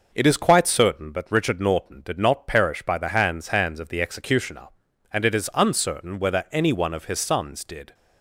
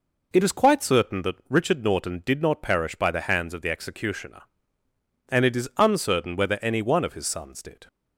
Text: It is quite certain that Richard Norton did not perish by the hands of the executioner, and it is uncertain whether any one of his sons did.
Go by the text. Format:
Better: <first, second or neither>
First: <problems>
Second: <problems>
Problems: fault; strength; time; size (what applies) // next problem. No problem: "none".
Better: second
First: says "hands" twice; at 3.4 s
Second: none